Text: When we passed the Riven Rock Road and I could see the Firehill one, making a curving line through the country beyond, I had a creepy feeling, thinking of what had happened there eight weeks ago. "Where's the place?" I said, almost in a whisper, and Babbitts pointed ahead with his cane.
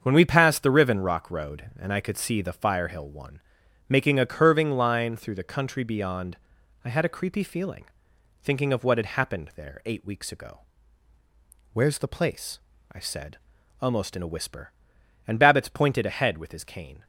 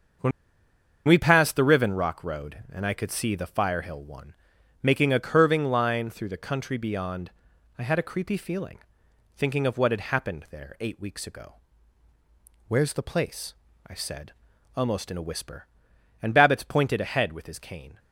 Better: first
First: starts louder than the rest; until 1.0 s; 7 dB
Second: starts louder than the rest; until 1.9 s; 6.5 dB // pauses between "When" and "we"; noticeable; at 0.3 s; 0.77 s long

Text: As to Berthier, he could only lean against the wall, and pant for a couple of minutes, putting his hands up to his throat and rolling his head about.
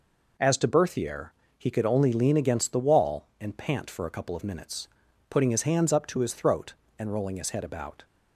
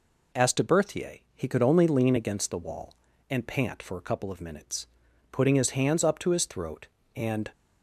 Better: first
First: none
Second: stops before "rolling his head about"; at 7.5 s

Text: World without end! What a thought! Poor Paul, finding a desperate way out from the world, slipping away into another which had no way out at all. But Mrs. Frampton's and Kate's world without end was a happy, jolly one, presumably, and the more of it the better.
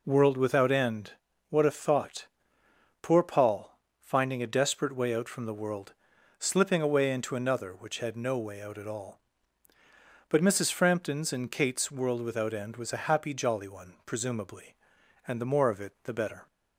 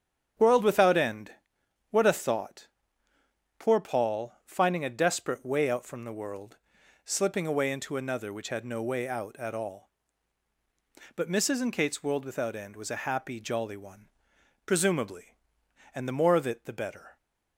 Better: first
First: none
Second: starts louder than the rest; strong; until 1.9 s; 8 dB // skips "Frampton's"; at 11.5 s

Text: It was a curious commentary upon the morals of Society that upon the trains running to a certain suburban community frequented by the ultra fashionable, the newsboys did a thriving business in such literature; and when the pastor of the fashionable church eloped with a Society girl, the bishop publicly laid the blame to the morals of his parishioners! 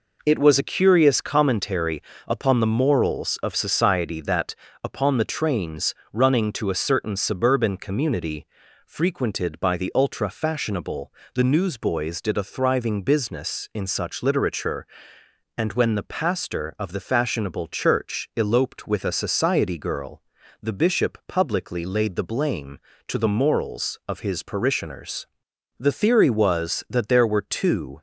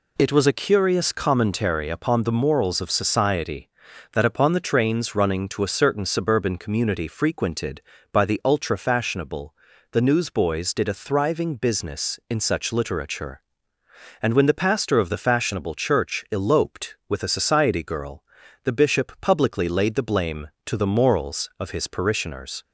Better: second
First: pauses between "commentary" and "upon"; slight; at 2.0 s; 0.26 s long // pauses between "that" and "upon"; slight; at 4.5 s; 0.30 s long // pauses between "trains" and "running"; slight; at 5.9 s; 0.16 s long // pauses between "community" and "frequented"; at 8.4 s; 0.40 s long // goes on to say "The theory was that there were two"; strong; from 25.7 s on; 2.2 s long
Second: none

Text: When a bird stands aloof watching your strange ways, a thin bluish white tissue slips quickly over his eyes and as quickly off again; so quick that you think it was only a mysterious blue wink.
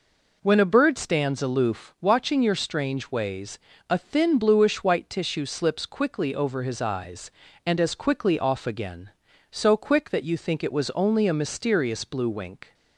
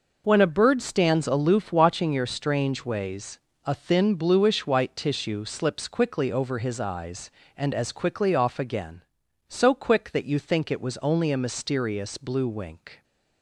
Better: neither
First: none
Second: none

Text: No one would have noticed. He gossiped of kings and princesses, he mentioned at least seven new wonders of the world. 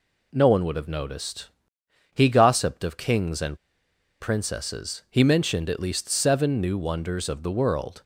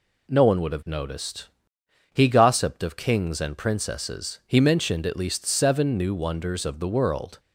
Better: second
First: pauses between "and" and "princesses"; noticeable; at 3.5 s; 0.63 s long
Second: none

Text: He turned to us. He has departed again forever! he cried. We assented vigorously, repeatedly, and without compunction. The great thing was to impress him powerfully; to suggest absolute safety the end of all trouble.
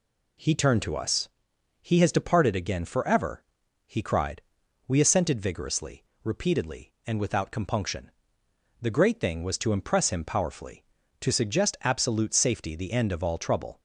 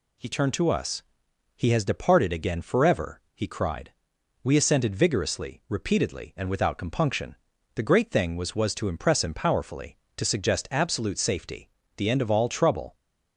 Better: first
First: none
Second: says "was" twice; at 8.5 s // pauses between "safety" and "the"; slight; at 11.6 s; 0.28 s long

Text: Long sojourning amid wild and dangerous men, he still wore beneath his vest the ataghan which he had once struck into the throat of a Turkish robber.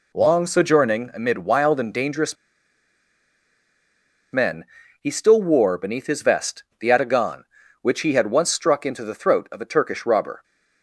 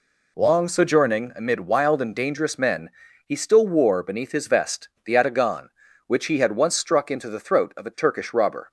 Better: second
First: pauses between "dangerous" and "men"; strong; at 2.3 s; 1.9 s long // pauses between "vest" and "the"; slight; at 6.6 s; 0.18 s long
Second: pauses between "vest" and "the"; slight; at 4.8 s; 0.18 s long

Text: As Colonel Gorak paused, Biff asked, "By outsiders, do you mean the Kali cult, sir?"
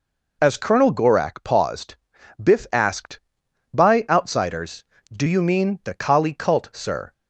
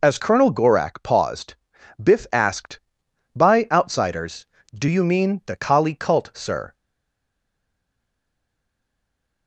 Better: first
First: none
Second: stays silent after the last word; strong; from 6.7 s on; 2.7 s long

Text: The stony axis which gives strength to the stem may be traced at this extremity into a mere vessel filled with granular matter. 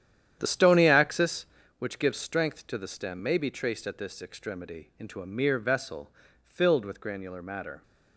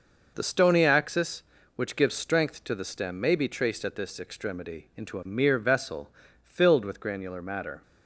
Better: second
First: starts louder than the rest; strong; until 1.7 s; 10 dB // pauses between "vessel" and "filled"; slight; at 6.0 s; 0.34 s long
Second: pauses between "vessel" and "filled"; slight; at 6.0 s; 0.34 s long

